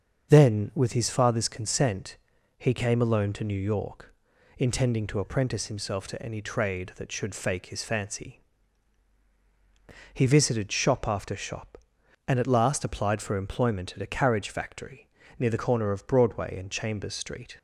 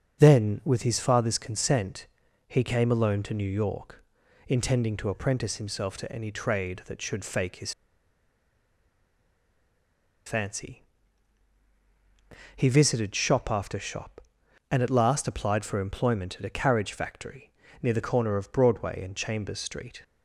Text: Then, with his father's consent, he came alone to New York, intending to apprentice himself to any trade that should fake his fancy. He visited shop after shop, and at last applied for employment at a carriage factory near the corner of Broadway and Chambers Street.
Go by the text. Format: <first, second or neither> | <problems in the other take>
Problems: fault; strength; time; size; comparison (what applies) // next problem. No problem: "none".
first | starts louder than the rest; until 1.2 s; 6.5 dB; also in the first // pauses between "his" and "fancy"; strong; at 7.7 s; 2.5 s long // pauses between "factory" and "near"; slight; at 17.5 s; 0.30 s long; slight in the first